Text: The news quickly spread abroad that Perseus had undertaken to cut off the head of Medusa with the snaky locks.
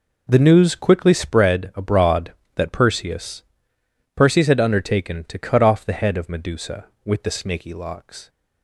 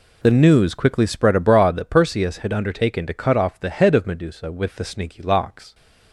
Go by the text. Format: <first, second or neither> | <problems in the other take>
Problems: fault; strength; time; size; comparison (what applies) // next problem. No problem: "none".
second | says "Perseus" twice; at 4.1 s